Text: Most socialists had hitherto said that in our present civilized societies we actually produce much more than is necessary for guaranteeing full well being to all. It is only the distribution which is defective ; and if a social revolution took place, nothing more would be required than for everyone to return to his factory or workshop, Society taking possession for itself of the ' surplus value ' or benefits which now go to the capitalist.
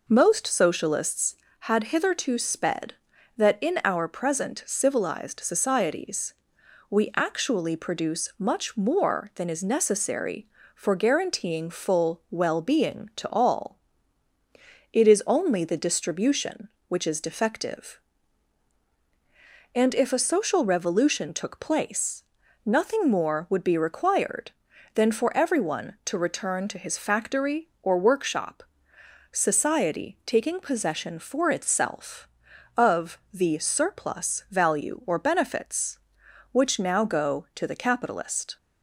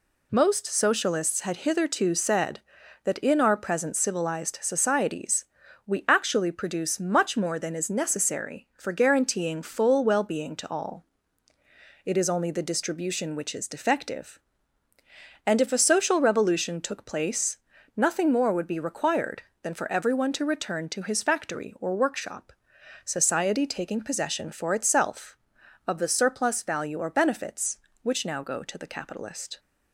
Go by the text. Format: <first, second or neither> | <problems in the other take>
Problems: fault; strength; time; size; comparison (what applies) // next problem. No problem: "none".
second | says "sped" for "said"; at 2.3 s // pauses between "societies" and "we"; noticeable; at 6.3 s; 0.56 s long; also in the second